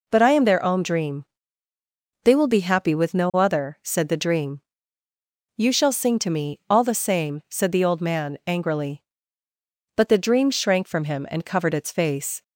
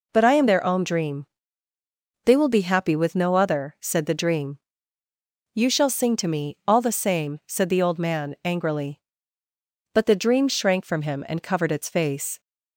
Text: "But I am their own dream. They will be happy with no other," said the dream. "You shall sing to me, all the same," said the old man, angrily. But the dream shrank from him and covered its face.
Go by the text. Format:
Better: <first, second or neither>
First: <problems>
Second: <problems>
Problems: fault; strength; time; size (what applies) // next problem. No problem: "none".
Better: neither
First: none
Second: none